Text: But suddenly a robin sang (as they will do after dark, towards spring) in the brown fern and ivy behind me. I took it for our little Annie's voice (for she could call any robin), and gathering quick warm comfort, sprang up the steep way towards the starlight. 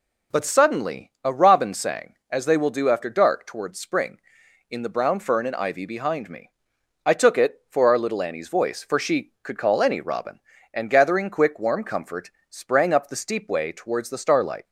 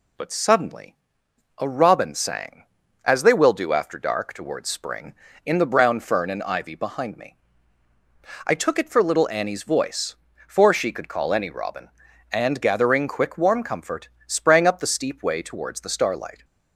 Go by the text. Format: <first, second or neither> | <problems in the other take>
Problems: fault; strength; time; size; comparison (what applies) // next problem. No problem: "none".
first | pauses between "suddenly" and "a"; noticeable; at 0.9 s; 0.64 s long // skips "our"; at 9.0 s